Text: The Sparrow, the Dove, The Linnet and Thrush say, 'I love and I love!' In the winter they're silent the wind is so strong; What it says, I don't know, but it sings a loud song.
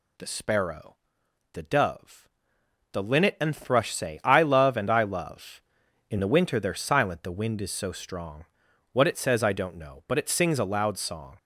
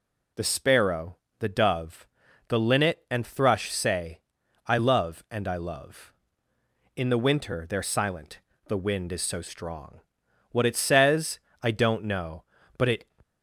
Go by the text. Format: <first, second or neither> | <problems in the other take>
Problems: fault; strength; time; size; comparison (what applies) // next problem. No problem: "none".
first | pauses between "silent" and "the"; slight; at 8.3 s; 0.28 s long // stops before "sings a loud song"; at 13.2 s